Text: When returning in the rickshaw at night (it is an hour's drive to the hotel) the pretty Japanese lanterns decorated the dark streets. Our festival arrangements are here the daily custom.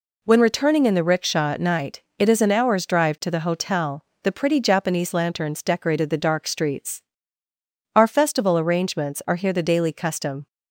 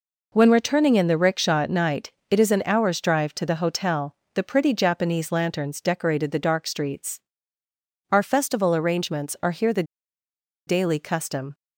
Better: first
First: none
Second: pauses between "the" and "daily"; noticeable; at 9.8 s; 0.84 s long

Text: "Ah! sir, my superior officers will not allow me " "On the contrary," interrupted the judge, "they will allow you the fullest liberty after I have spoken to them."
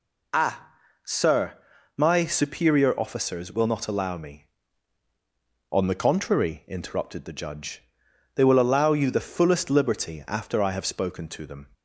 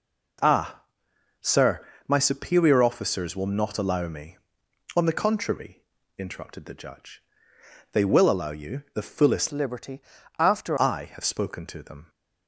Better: first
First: none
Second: changes voice from "liberty" to "after"; from 9.5 to 10.7 s; 1.2 s long // pauses between "liberty" and "after"; at 10.0 s; 0.38 s long

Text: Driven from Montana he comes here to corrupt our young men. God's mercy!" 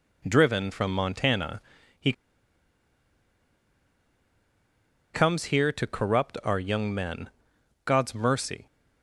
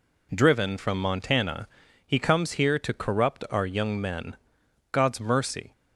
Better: second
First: pauses between "Montana" and "he"; at 1.5 s; 0.40 s long // pauses between "he" and "comes"; strong; at 2.1 s; 3.0 s long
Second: pauses between "Montana" and "he"; at 1.6 s; 0.40 s long

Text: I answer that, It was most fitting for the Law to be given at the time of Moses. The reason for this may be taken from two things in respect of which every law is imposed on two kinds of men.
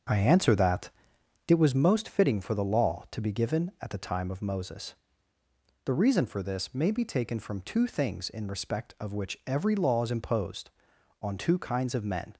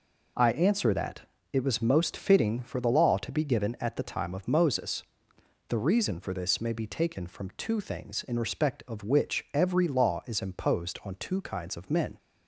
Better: second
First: starts louder than the rest; until 1.8 s; 7 dB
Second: none

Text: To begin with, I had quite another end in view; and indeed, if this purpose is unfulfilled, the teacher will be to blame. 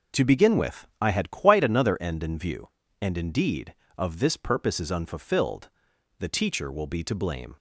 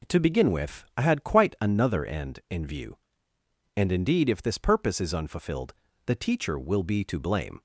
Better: second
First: says "of" for "if"; at 3.9 s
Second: none

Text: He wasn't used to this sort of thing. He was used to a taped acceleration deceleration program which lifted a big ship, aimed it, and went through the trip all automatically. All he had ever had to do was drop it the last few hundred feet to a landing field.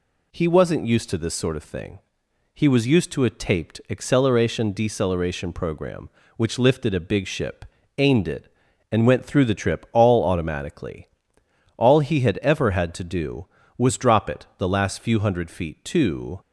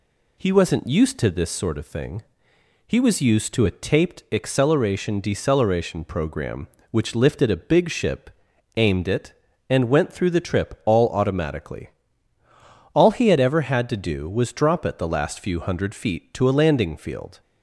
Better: second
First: stops before "a landing field"; at 16.4 s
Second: none

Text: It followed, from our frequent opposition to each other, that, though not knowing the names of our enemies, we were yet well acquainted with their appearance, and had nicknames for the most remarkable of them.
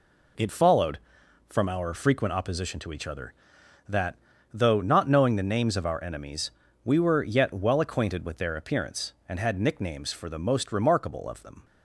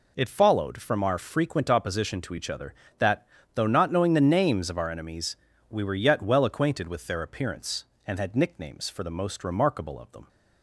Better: neither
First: none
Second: none

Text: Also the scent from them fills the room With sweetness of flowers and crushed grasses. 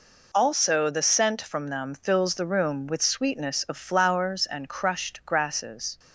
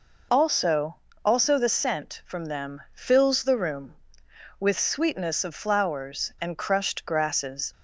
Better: first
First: none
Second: says "Also" twice; at 1.2 s

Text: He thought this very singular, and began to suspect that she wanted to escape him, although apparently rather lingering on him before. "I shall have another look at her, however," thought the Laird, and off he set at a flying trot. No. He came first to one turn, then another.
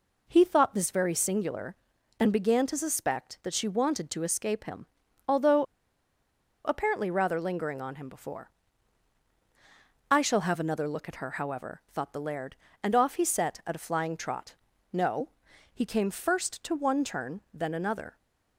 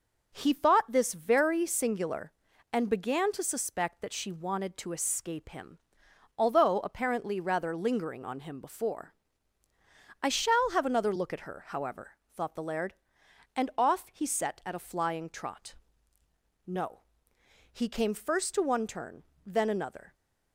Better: second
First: pauses between "although" and "apparently"; at 5.6 s; 1.0 s long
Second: none

